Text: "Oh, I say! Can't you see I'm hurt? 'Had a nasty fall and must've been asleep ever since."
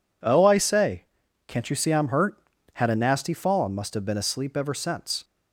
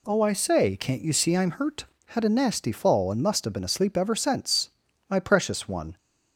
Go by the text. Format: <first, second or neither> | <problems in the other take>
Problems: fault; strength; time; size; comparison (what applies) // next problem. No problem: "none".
first | goes on to say "My precious one"; noticeable; from 5.0 s on; 0.88 s long